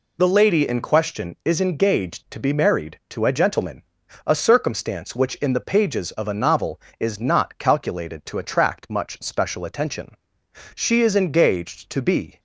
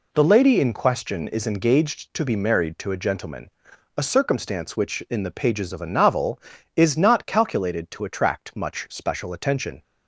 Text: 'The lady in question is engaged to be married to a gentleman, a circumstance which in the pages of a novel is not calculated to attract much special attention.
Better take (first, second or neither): second